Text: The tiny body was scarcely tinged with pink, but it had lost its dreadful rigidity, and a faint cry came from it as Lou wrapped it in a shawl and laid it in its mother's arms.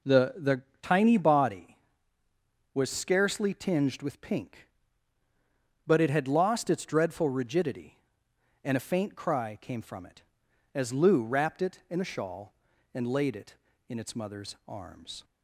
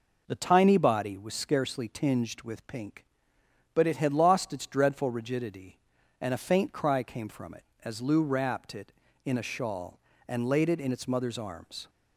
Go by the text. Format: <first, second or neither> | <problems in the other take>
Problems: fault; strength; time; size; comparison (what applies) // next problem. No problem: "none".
second | says "The" twice; at 0.3 s